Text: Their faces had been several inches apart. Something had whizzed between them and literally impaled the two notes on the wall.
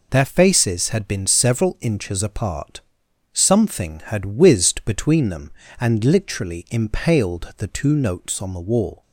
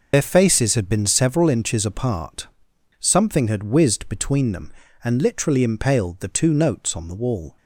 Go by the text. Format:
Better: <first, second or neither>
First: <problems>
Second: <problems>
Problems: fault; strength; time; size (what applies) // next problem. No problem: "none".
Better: first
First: none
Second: loses the start of "Their"; at 0.1 s; 70 ms